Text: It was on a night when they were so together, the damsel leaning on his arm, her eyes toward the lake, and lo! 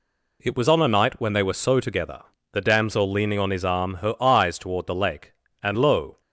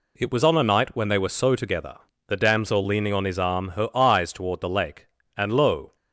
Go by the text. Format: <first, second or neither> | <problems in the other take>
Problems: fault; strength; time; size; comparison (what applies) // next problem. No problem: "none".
neither | none